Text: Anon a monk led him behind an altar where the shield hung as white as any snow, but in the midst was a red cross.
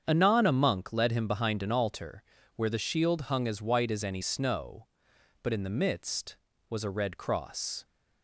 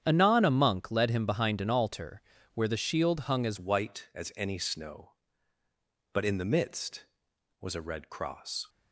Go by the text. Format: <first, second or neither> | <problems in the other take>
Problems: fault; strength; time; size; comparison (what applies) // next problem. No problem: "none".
first | starts louder than the rest; strong; until 1.0 s; 9.5 dB; strong in the first // pauses between "altar" and "where"; slight; at 2.2 s; 0.34 s long; slight in the first // changes voice at "white"; from 3.5 s on; 5.1 s long